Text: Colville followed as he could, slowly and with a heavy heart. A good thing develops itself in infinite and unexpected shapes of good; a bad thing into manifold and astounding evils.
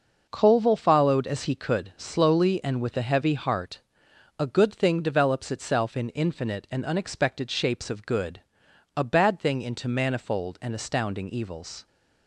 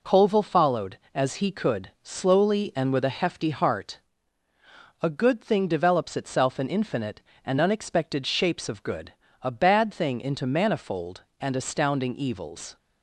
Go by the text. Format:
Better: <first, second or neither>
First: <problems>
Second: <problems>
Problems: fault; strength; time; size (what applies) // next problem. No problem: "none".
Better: first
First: none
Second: says "hefty" for "heavy"; at 3.1 s